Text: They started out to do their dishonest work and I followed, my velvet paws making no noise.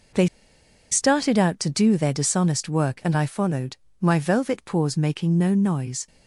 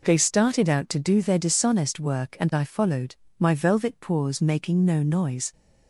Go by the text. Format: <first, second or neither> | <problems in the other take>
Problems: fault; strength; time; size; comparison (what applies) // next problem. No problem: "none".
second | pauses between "They" and "started"; noticeable; at 0.2 s; 0.63 s long